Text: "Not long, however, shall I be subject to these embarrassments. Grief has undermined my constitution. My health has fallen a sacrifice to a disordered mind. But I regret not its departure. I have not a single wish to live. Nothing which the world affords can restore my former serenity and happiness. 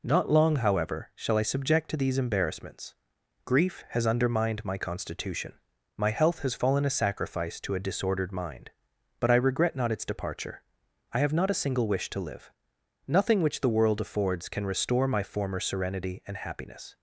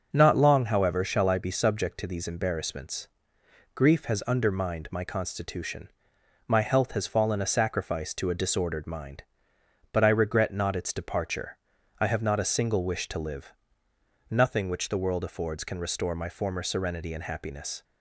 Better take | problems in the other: second | skips "be"; at 1.4 s

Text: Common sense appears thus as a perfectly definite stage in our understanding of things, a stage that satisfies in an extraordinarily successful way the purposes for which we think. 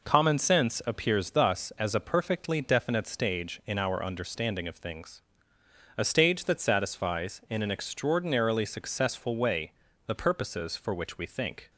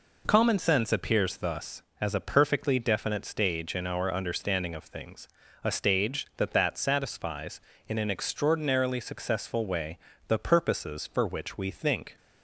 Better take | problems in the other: first | says "that" twice; at 6.5 s // pauses between "way" and "the"; slight; at 9.9 s; 0.28 s long; slight in the first

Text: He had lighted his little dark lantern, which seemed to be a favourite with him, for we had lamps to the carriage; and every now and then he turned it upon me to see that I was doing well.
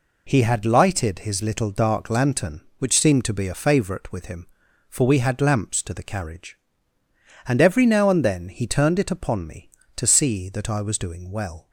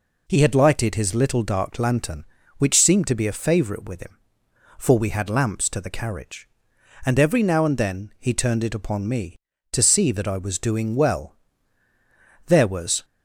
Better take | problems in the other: first | goes on to say "There was"; from 12.4 s on; 0.58 s long

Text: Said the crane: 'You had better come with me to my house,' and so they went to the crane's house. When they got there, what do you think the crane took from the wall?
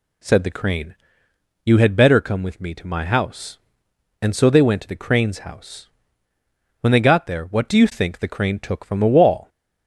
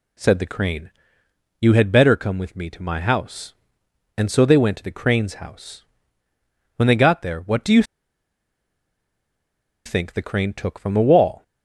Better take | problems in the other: first | pauses between "you" and "think"; strong; at 7.8 s; 2.0 s long

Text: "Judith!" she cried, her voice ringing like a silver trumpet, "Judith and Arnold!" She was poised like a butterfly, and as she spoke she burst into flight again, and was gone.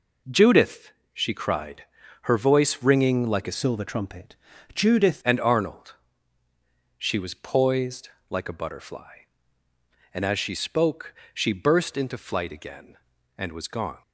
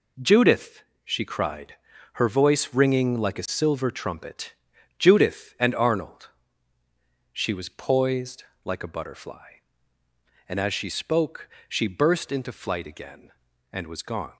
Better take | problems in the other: second | changes voice from "silver" to "Judith"; from 3.5 to 5.2 s; 1.7 s long // pauses between "poised" and "like"; slight; at 8.0 s; 0.18 s long; slight in the second // pauses between "spoke" and "she"; slight; at 11.1 s; 0.20 s long; slight in the second

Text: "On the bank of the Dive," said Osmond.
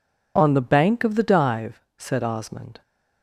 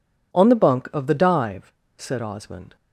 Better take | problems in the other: first | says "bunk" for "bank"; at 0.5 s

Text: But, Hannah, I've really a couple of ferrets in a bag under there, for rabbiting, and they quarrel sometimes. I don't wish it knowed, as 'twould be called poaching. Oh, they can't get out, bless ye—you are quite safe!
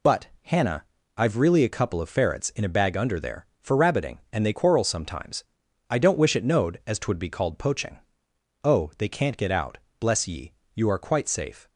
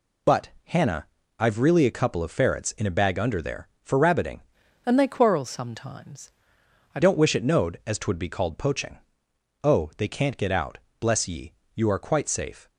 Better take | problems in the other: first | changes voice from "and" to "I"; from 4.8 to 7.0 s; 2.2 s long

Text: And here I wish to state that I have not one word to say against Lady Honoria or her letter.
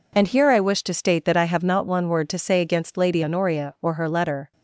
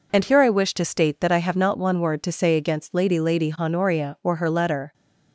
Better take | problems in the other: first | says "Lady" twice; at 3.1 s

